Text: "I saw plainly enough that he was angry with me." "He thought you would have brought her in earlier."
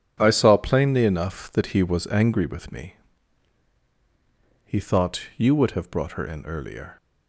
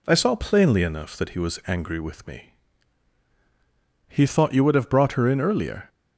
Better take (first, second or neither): neither